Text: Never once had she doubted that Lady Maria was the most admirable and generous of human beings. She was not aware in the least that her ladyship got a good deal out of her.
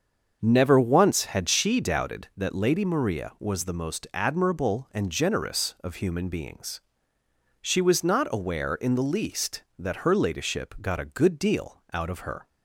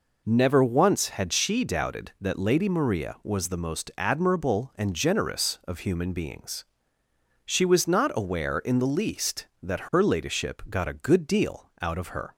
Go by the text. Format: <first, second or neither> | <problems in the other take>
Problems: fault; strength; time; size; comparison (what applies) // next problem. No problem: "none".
second | starts louder than the rest; until 2.3 s; 6.5 dB